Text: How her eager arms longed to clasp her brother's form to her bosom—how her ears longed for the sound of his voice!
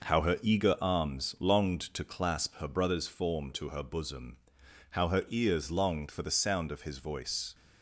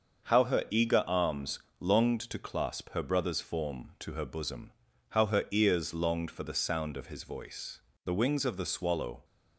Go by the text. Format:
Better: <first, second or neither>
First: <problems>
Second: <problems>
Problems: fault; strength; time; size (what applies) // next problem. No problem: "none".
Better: first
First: none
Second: starts louder than the rest; until 1.3 s; 6.5 dB // pauses between "arms" and "longed"; slight; at 1.5 s; 0.22 s long // goes on to say "The wings of the swallow"; noticeable; from 8.0 s on; 1.1 s long